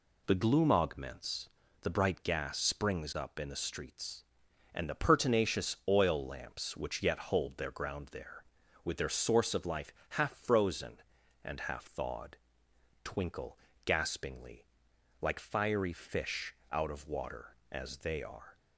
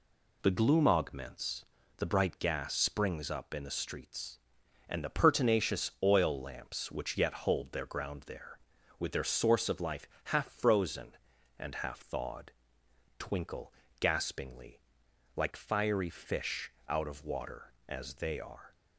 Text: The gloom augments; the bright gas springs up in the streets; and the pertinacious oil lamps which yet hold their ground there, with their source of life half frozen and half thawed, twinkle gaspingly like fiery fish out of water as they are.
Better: neither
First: pauses between "life" and "half"; slight; at 9.9 s; 0.20 s long // pauses between "twinkle" and "gaspingly"; slight; at 13.5 s; 0.26 s long // pauses between "gaspingly" and "like"; noticeable; at 14.6 s; 0.56 s long // pauses between "fish" and "out"; slight; at 16.5 s; 0.16 s long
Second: pauses between "life" and "half"; slight; at 10.0 s; 0.20 s long // pauses between "twinkle" and "gaspingly"; slight; at 13.7 s; 0.26 s long // pauses between "gaspingly" and "like"; noticeable; at 14.7 s; 0.56 s long // pauses between "fish" and "out"; slight; at 16.7 s; 0.16 s long

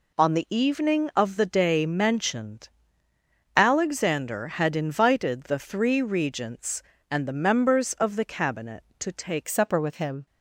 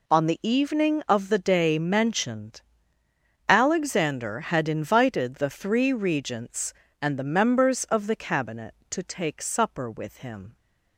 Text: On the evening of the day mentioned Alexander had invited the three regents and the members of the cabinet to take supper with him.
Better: second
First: pauses between "mentioned" and "Alexander"; noticeable; at 2.6 s; 0.88 s long // changes voice at "supper"; from 9.4 s on; 0.8 s long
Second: pauses between "mentioned" and "Alexander"; noticeable; at 2.6 s; 0.88 s long

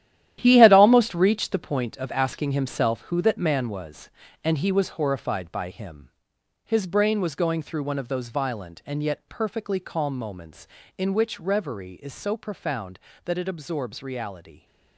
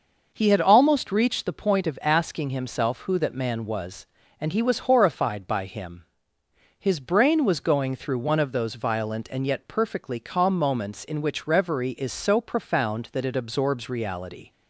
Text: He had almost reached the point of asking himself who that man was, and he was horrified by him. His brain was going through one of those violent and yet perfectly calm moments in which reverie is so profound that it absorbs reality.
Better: second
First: gets quieter; strong; throughout; 11 dB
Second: none

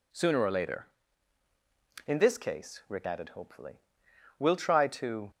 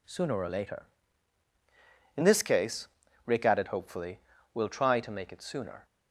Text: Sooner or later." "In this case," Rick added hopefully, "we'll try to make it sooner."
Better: second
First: stops before "make it sooner"; at 5.3 s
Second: none

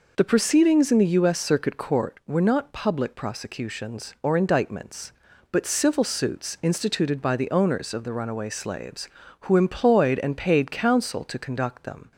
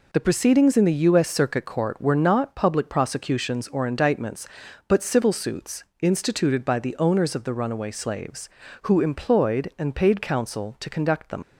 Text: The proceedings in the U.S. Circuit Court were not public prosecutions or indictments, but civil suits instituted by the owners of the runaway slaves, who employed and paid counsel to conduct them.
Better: first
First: none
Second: pauses between "suits" and "instituted"; slight; at 5.8 s; 0.16 s long // leaves "them" unfinished; at 11.4 s; 85 ms

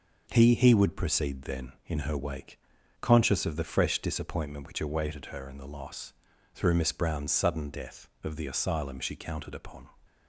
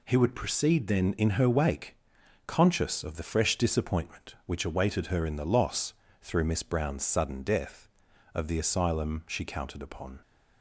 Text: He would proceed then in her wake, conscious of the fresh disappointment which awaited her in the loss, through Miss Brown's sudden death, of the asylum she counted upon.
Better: second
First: says "He" twice; at 0.5 s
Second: none

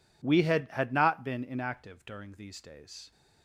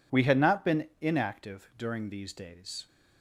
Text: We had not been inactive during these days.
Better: second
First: says "had" twice; at 0.7 s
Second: none

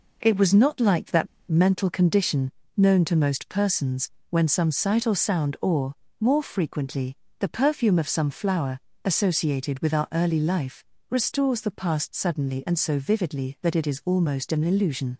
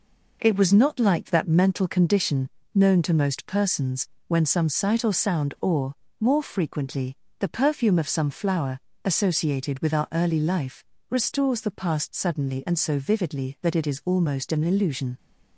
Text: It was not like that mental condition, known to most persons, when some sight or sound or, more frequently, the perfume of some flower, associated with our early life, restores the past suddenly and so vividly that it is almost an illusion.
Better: second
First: pauses between "that" and "mental"; slight; at 1.2 s; 0.21 s long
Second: none

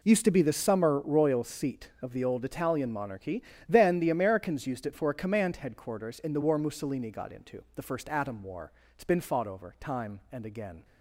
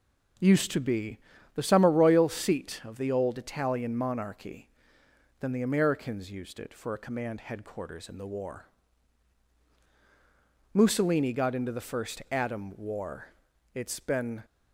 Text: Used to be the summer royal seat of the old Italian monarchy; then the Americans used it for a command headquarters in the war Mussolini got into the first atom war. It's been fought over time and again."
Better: first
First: none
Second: pauses between "be" and "the"; at 1.1 s; 0.38 s long // pauses between "war" and "Mussolini"; strong; at 8.6 s; 2.0 s long // stops before "fought over time and again"; at 14.4 s

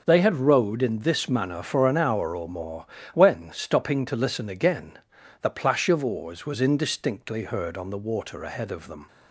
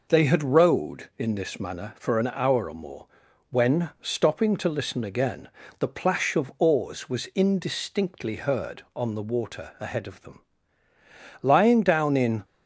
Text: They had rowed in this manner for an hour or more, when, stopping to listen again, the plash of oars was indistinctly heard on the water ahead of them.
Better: first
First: none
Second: goes on to say "Lying down in"; noticeable; from 11.4 s on; 1.0 s long

